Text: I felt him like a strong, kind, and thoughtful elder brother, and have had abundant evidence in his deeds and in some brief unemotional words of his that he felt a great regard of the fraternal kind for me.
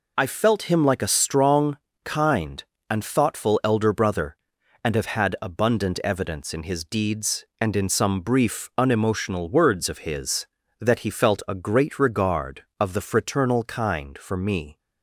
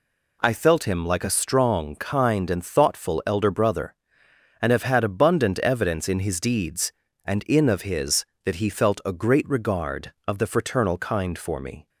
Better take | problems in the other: first | skips "some brief unemotional words"; at 7.6 s

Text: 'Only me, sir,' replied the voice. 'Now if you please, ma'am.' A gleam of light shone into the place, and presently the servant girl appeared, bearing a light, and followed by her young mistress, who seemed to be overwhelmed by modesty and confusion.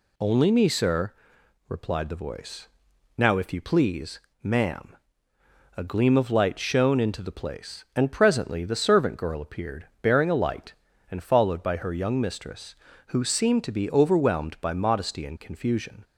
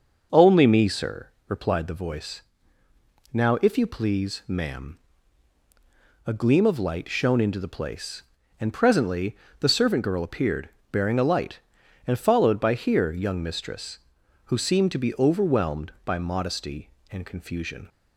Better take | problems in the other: first | starts louder than the rest; noticeable; until 1.5 s; 6 dB // pauses between "presently" and "the"; slight; at 9.3 s; 0.24 s long // says "here" for "her"; at 12.7 s

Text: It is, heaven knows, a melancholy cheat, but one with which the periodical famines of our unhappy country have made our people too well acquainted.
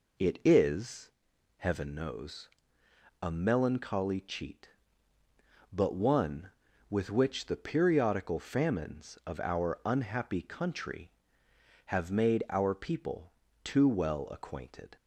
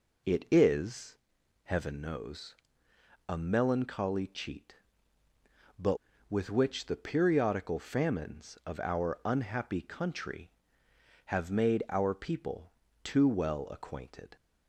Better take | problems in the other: first | skips "one"; at 6.1 s // pauses between "people" and "too"; slight; at 12.7 s; 0.28 s long; slight in the first

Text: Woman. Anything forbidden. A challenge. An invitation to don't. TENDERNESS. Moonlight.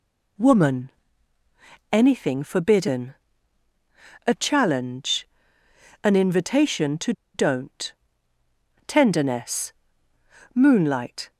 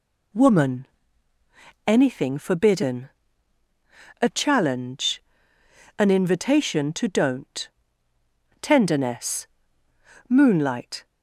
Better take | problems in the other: second | pauses between "to" and "don't"; slight; at 7.1 s; 0.22 s long

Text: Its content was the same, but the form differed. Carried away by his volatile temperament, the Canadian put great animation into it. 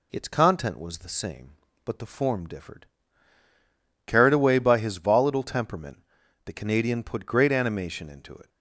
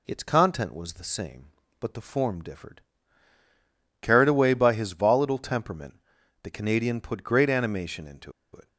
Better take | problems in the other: first | pauses between "into" and "it"; slight; at 8.3 s; 0.21 s long

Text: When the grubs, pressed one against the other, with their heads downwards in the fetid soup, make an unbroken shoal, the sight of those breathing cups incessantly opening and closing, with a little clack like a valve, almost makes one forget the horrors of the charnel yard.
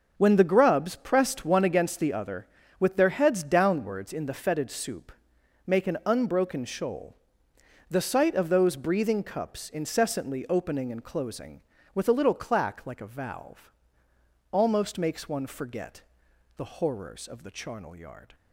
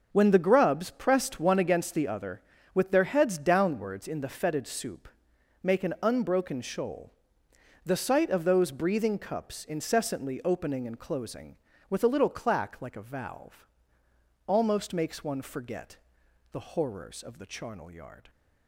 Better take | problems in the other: neither | starts louder than the rest; noticeable; the same in both // pauses between "forget" and "the"; noticeable; the same in both

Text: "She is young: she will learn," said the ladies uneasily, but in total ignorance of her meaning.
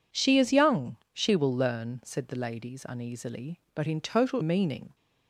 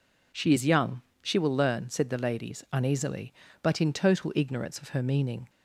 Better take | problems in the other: second | skips "ignorance of her"; at 4.4 s

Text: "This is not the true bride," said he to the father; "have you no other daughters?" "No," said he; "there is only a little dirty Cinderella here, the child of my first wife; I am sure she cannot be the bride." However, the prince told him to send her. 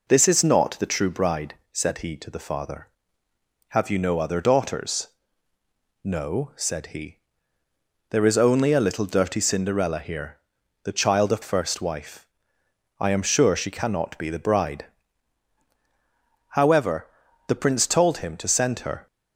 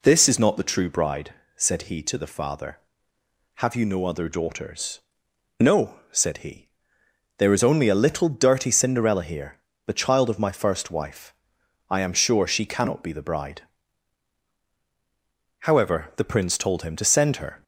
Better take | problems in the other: second | skips "my"; at 11.4 s

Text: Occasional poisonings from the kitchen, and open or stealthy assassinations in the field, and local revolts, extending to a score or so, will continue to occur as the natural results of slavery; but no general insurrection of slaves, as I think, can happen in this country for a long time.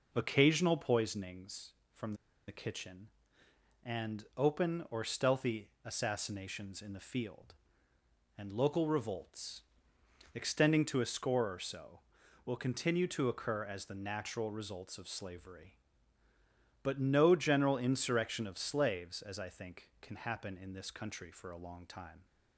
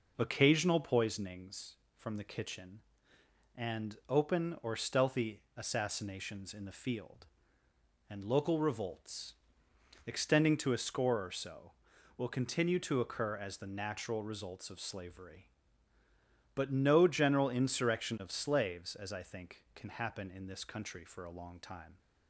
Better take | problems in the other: second | pauses between "from" and "the"; slight; at 2.1 s; 0.34 s long

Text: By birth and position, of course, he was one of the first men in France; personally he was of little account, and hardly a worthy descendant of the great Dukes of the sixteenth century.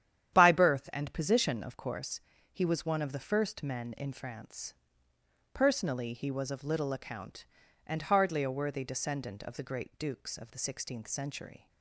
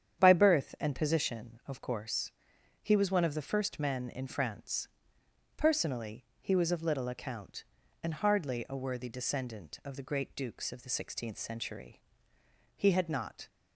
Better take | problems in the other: first | starts louder than the rest; strong; until 1.2 s; 9 dB; strong in the first // pauses between "personally" and "he"; slight; at 6.2 s; 0.16 s long // goes on to say "He had not"; noticeable; from 12.7 s on; 0.72 s long

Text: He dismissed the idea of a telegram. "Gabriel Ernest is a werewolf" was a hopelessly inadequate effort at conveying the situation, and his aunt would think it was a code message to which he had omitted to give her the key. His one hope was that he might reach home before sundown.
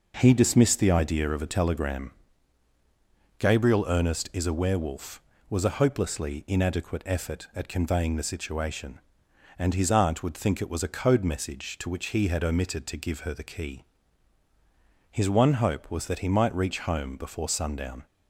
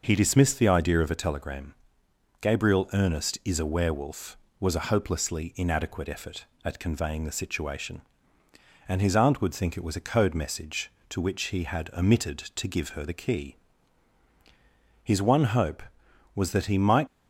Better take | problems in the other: first | stops before "reach home before sundown"; at 17.0 s

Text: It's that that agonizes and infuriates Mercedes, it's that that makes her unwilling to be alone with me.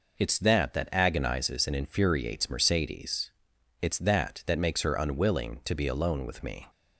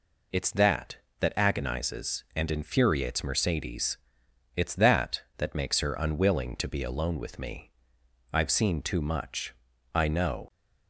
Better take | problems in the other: first | goes on to say "I've seen too much I know"; strong; from 8.3 s on; 2.1 s long

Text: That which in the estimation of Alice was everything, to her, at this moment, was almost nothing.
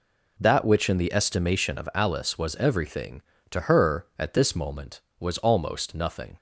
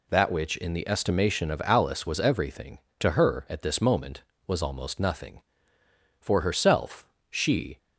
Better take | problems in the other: first | goes on to say "For herself she"; from 6.1 s on; 1.5 s long

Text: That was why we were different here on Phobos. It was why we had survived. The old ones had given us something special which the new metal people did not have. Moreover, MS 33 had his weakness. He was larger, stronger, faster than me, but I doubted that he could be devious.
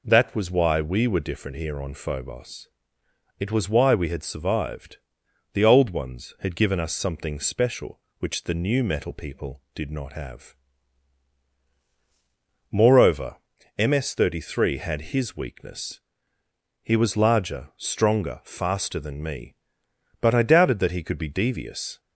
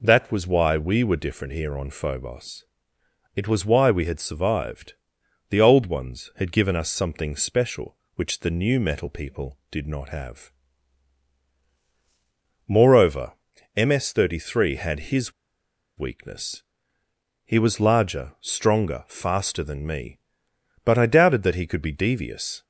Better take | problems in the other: first | pauses between "his" and "weakness"; noticeable; at 15.3 s; 0.67 s long

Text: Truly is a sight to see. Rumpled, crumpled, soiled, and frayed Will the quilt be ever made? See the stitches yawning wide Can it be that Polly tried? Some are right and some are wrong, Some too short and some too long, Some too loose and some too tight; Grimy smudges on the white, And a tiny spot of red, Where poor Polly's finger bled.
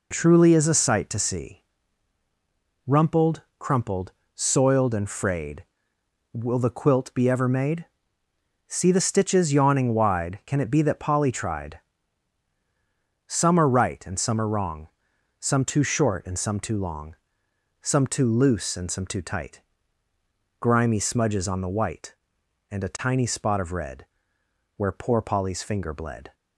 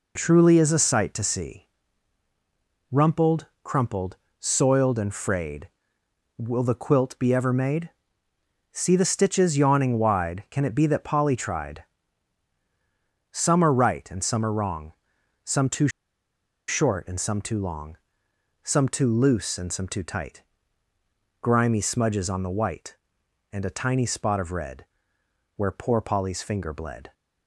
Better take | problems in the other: first | pauses between "too" and "short"; noticeable; at 15.8 s; 0.79 s long

